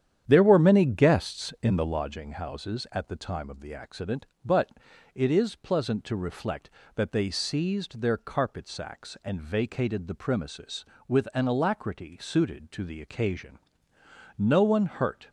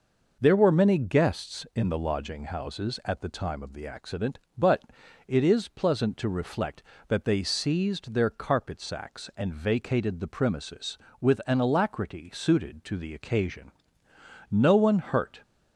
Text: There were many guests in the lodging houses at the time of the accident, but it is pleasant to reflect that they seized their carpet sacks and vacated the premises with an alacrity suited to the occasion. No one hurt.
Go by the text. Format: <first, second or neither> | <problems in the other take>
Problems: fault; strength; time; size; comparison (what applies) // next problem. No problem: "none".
second | starts louder than the rest; strong; until 2.0 s; 9.5 dB // pauses between "but" and "it"; at 4.6 s; 0.44 s long; also in the second